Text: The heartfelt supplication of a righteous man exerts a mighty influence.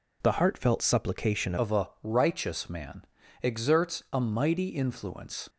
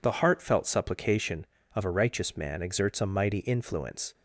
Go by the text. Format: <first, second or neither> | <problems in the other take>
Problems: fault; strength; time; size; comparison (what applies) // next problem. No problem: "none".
second | changes voice at "of"; from 1.5 s on; 3.9 s long // pauses between "man" and "exerts"; slight; at 3.0 s; 0.36 s long